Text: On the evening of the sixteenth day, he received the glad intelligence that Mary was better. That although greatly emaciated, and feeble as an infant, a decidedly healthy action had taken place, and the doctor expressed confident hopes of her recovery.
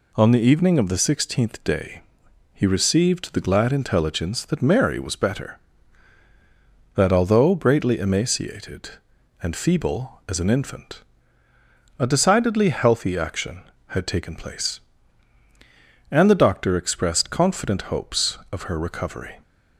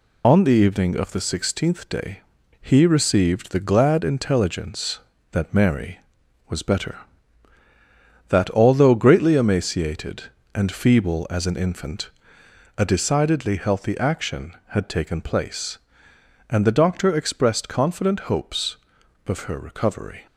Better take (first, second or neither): first